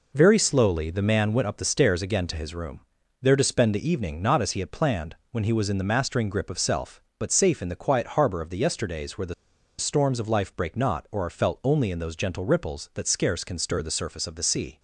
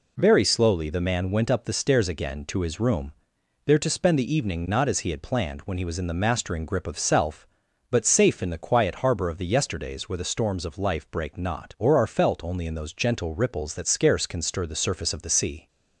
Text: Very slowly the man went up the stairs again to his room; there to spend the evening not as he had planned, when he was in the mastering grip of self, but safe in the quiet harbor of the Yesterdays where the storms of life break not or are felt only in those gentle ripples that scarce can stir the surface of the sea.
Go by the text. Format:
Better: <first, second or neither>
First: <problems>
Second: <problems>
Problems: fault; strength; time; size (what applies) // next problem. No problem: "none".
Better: second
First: pauses between "the" and "storms"; at 9.3 s; 0.45 s long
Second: none